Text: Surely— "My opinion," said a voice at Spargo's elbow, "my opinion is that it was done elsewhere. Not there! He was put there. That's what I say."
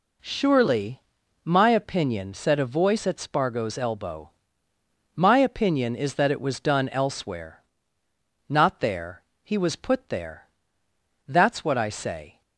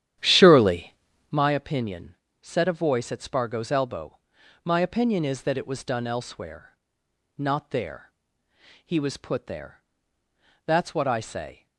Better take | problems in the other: first | starts louder than the rest; strong; until 1.5 s; 11 dB

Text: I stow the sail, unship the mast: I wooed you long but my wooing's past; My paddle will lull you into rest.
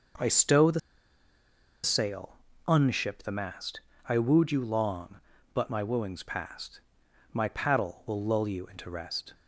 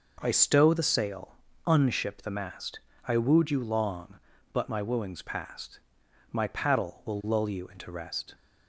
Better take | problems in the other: second | pauses between "the" and "sail"; at 0.7 s; 1.0 s long

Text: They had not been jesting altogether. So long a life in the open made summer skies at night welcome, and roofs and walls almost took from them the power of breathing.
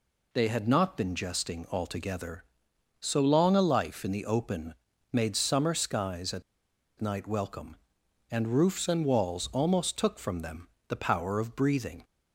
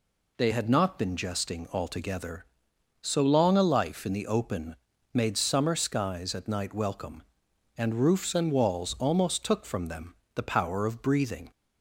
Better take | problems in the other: second | pauses between "open" and "made"; slight; at 4.7 s; 0.36 s long; slight in the second // pauses between "at" and "night"; noticeable; at 6.4 s; 0.57 s long // pauses between "them" and "the"; slight; at 10.6 s; 0.22 s long; slight in the second

